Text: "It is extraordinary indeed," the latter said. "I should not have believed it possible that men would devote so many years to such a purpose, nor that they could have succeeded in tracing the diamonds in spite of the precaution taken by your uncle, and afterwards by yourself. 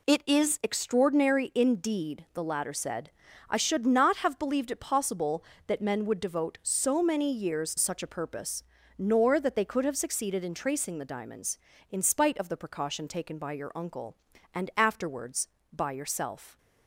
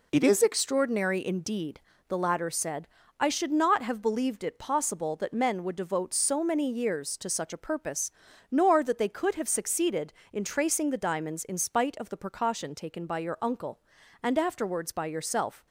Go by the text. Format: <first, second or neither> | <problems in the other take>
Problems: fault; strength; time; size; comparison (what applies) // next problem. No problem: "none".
second | skips "to"; at 7.7 s